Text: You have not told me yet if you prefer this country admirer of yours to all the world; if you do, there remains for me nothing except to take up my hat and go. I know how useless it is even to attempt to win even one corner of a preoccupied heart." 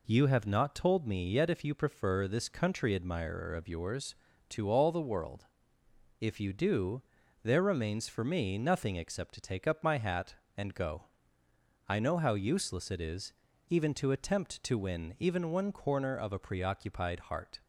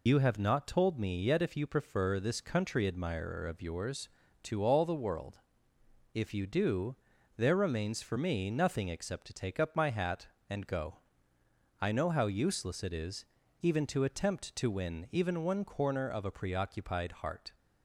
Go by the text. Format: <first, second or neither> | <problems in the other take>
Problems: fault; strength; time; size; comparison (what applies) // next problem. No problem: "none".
first | loses the start of "You"; at 0.0 s; 90 ms // pauses between "is" and "even"; at 13.2 s; 0.38 s long; also in the first